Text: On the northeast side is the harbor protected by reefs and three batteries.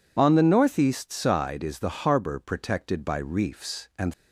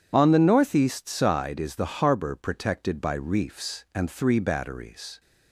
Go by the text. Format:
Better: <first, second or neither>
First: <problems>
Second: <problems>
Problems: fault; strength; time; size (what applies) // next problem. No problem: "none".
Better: second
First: stops before "three batteries"; at 4.1 s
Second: none